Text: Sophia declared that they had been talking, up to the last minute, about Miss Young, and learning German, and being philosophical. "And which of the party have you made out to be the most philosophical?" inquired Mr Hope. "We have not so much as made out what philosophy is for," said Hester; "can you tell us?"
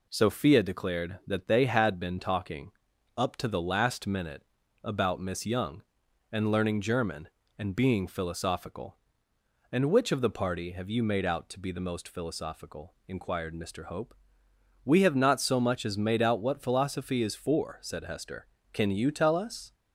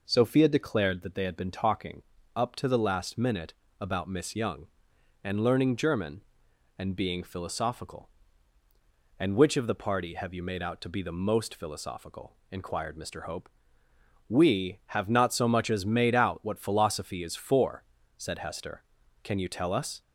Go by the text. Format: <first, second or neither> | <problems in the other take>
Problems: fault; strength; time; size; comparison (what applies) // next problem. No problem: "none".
neither | none